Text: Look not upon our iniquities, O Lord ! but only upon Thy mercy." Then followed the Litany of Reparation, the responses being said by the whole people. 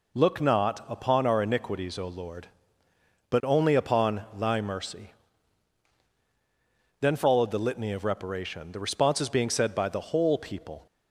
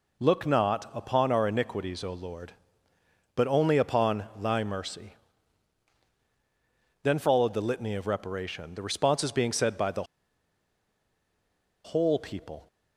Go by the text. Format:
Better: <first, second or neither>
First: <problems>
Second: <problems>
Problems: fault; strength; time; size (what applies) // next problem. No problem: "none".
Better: first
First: none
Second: pauses between "the" and "whole"; strong; at 10.0 s; 1.7 s long